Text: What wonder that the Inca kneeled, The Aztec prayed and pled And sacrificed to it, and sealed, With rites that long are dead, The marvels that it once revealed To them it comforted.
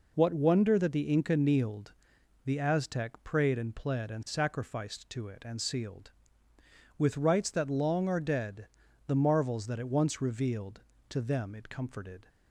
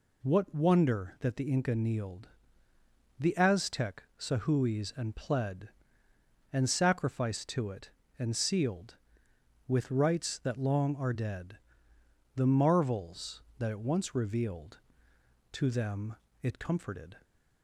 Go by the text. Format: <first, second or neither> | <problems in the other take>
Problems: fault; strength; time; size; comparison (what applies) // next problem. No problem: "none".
first | says "sahuis" for "prayed"; at 4.1 s // pauses between "them" and "it"; slight; at 16.1 s; 0.26 s long